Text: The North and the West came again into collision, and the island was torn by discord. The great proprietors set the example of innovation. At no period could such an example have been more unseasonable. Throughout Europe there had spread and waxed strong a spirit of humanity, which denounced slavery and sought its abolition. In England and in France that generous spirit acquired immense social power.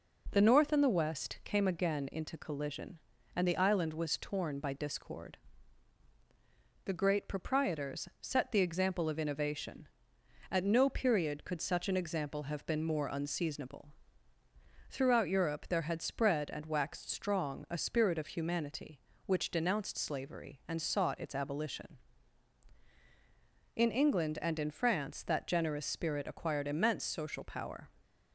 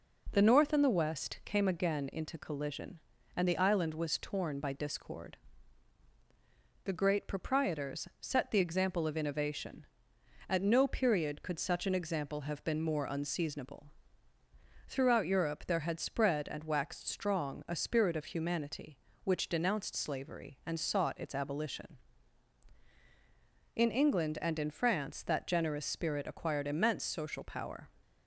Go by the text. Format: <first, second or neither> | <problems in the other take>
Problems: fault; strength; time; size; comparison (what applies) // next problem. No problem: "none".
neither | none